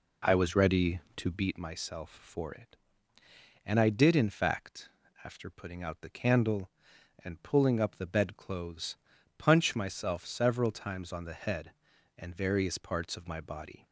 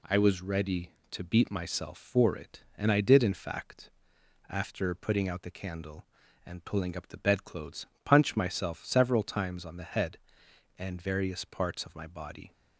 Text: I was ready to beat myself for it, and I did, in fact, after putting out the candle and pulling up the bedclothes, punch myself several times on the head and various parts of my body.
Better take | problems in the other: second | starts louder than the rest; slight; until 1.5 s; 3 dB

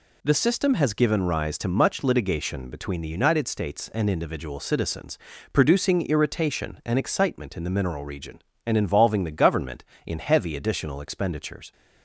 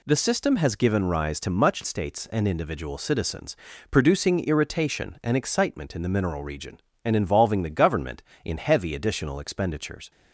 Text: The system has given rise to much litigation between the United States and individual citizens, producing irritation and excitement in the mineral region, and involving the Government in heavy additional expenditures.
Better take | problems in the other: first | skips "litigation between the United"; at 1.8 s

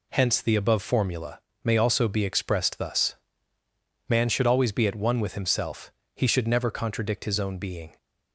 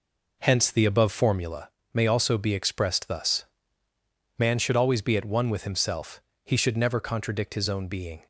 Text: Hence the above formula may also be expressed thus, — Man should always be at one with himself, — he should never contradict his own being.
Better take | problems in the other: first | starts louder than the rest; noticeable; until 1.4 s; 4.5 dB // pauses between "formula" and "may"; slight; at 1.6 s; 0.24 s long; slight in the first

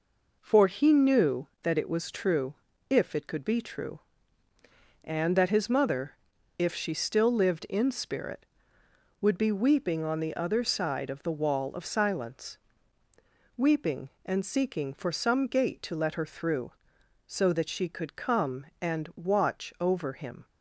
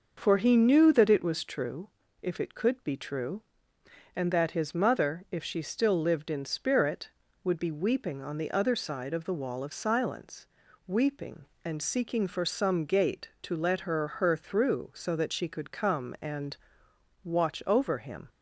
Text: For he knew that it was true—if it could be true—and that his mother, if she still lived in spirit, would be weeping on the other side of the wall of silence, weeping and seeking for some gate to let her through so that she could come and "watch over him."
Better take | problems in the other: first | says "her" twice; at 14.0 s // pauses between "and" and "watch"; noticeable; at 16.5 s; 0.66 s long

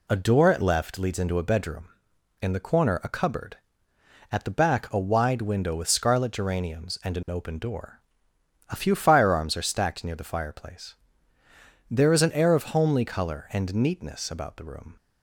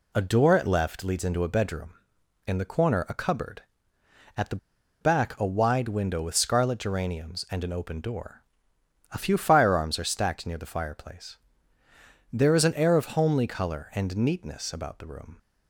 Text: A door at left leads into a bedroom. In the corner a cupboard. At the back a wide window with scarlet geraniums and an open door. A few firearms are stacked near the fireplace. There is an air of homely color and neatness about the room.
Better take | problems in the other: first | pauses between "the" and "back"; at 4.5 s; 0.44 s long

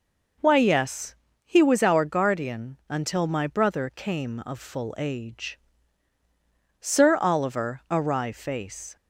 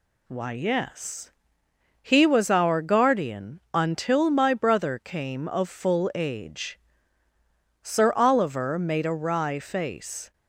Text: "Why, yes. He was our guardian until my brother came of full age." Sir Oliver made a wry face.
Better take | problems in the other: second | skips "made"; at 7.8 s

